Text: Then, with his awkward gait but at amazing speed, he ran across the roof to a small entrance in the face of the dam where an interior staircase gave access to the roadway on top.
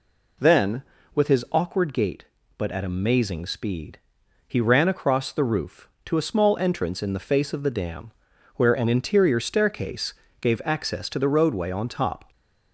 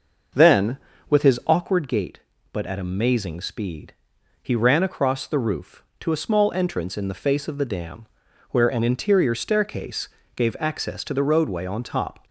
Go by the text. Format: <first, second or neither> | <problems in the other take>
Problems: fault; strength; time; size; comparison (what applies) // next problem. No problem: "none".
first | starts louder than the rest; noticeable; until 1.9 s; 6 dB // pauses between "dam" and "where"; at 8.0 s; 0.44 s long; also in the first // pauses between "staircase" and "gave"; slight; at 10.0 s; 0.26 s long; slight in the first